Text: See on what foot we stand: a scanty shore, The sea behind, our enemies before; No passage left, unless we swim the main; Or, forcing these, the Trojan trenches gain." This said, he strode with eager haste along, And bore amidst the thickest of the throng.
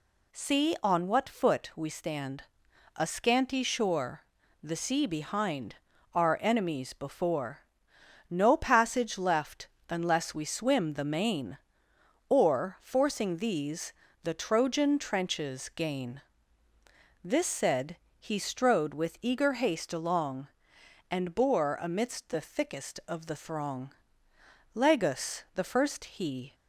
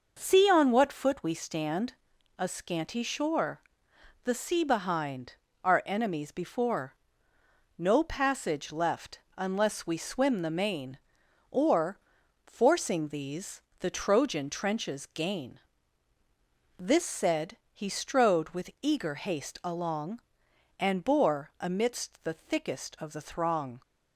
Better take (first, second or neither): second